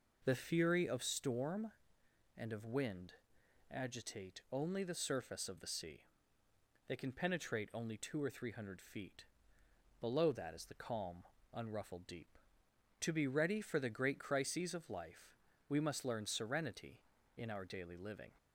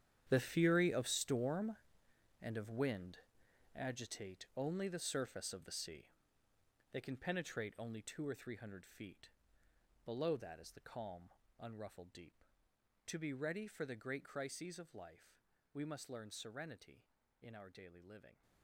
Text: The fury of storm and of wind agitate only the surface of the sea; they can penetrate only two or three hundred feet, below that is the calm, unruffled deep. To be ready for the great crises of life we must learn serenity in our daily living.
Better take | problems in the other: first | gets quieter; strong; throughout; 16 dB // pauses between "wind" and "agitate"; noticeable; at 3.1 s; 0.58 s long; noticeable in the first // pauses between "life" and "we"; slight; at 15.4 s; 0.28 s long; slight in the first

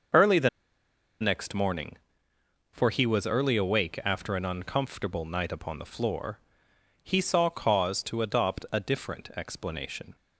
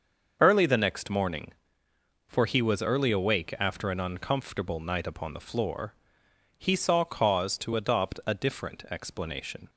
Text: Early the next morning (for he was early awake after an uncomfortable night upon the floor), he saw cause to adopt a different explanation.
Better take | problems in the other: second | starts louder than the rest; until 1.8 s; 6 dB; also in the second // pauses between "the" and "next"; noticeable; at 0.4 s; 0.71 s long

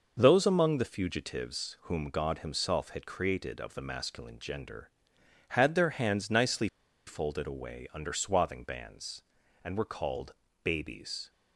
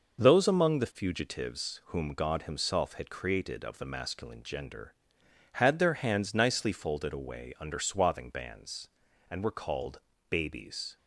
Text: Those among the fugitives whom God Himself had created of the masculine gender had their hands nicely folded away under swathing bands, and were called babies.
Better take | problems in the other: second | pauses between "nicely" and "folded"; at 6.6 s; 0.40 s long // pauses between "called" and "babies"; slight; at 10.3 s; 0.32 s long; slight in the second

